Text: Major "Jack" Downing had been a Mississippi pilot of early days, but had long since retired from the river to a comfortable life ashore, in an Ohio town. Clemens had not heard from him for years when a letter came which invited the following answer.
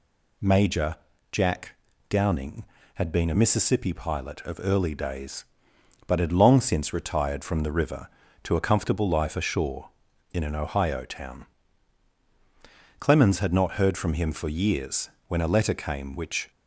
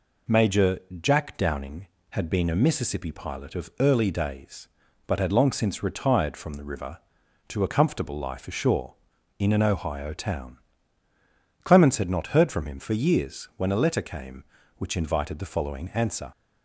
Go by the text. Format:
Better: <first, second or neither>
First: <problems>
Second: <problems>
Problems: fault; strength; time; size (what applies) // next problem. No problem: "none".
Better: second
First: pauses between "Major" and "Jack"; slight; at 0.9 s; 0.36 s long // pauses between "Jack" and "Downing"; slight; at 1.7 s; 0.36 s long // pauses between "years" and "when"; slight; at 15.0 s; 0.20 s long // stops before "invited the following answer"; at 16.5 s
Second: pauses between "Major" and "Jack"; slight; at 0.7 s; 0.24 s long